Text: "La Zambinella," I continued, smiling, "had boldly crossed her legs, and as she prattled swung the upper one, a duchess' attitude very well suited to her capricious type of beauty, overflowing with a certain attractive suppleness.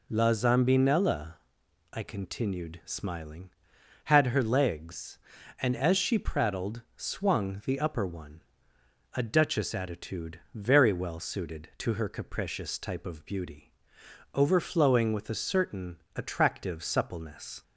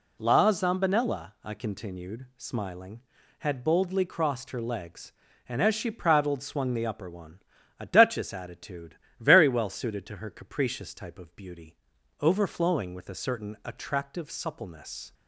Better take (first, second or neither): second